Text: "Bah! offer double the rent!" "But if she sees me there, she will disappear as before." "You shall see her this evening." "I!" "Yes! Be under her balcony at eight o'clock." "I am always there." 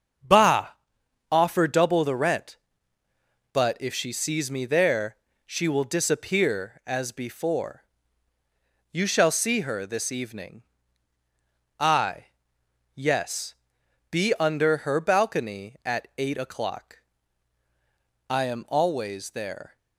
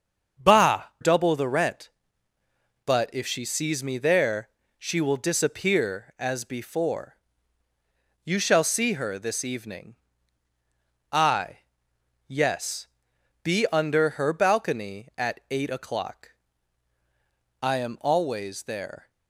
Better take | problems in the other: first | starts louder than the rest; until 1.5 s; 6.5 dB; also in the first // skips "offer"; at 0.9 s

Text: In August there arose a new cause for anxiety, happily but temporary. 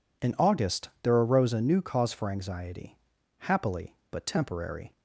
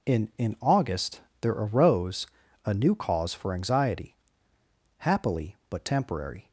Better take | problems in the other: first | says "In" twice; at 0.3 s // pauses between "August" and "there"; slight; at 1.1 s; 0.22 s long // pauses between "arose" and "a"; at 2.2 s; 0.38 s long

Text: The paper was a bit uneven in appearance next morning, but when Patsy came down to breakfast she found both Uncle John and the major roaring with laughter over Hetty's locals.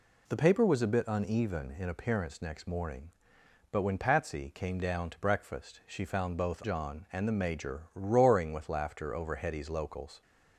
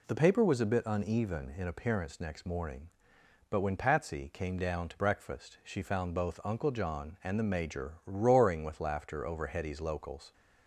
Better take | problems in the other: second | skips "Uncle"; at 6.6 s

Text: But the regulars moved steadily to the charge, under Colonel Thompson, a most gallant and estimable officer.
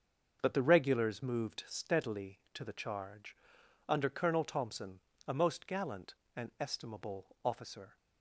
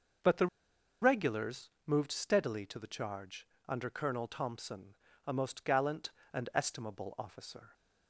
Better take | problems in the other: first | starts louder than the rest; noticeable; until 1.9 s; 6 dB; also in the first // pauses between "the" and "regulars"; noticeable; at 0.4 s; 0.55 s long // pauses between "regulars" and "moved"; slight; at 1.6 s; 0.16 s long

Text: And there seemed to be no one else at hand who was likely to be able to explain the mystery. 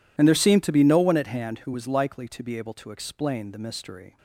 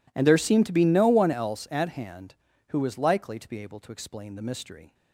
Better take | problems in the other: second | skips "else"; at 1.1 s

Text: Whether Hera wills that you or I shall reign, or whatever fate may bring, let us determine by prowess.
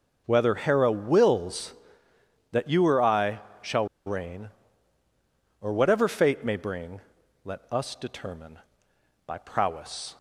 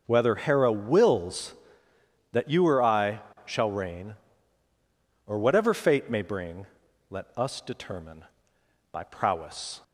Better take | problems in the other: second | pauses between "I" and "shall"; slight; at 3.3 s; 0.20 s long; slight in the second // pauses between "shall" and "reign"; slight; at 3.8 s; 0.20 s long

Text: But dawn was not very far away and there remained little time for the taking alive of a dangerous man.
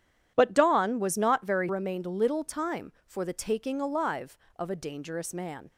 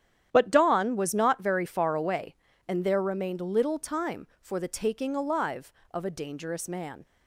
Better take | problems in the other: second | starts louder than the rest; strong; until 1.3 s; 10 dB; strong in the second // skips "far away and there"; at 1.6 s

